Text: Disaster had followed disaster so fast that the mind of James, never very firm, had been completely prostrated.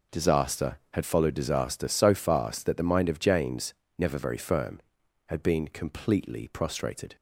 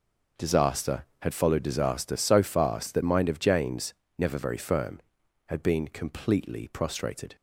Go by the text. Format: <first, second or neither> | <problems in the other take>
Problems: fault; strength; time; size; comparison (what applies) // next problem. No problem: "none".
first | skips "the"; at 3.0 s